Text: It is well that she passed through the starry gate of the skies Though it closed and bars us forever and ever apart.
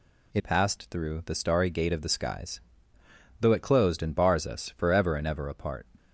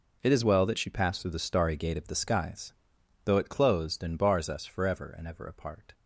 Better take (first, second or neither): second